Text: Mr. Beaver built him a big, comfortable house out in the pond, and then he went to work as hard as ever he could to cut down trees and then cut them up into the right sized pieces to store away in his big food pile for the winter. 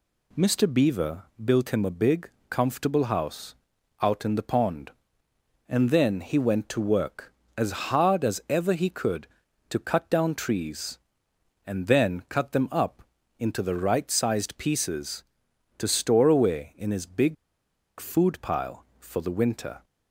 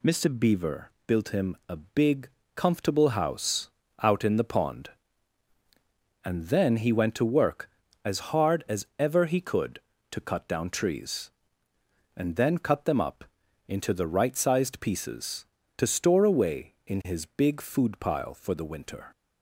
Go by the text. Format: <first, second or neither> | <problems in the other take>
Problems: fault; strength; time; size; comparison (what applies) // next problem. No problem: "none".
second | pauses between "Beaver" and "built"; slight; at 1.2 s; 0.20 s long; slight in the second // pauses between "house" and "out"; noticeable; at 3.5 s; 0.48 s long; slight in the second // pauses between "up" and "into"; at 13.0 s; 0.38 s long; also in the second // pauses between "big" and "food"; noticeable; at 17.3 s; 0.64 s long